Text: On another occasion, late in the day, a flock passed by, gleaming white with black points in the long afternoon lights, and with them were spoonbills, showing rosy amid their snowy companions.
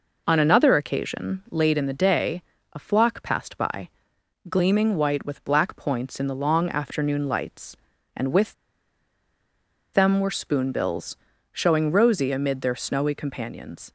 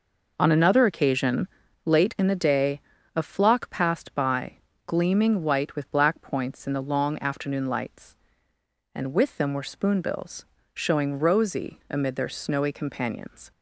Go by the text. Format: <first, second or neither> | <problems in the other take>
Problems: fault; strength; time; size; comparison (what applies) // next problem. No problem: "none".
second | pauses between "with" and "them"; strong; at 8.5 s; 1.3 s long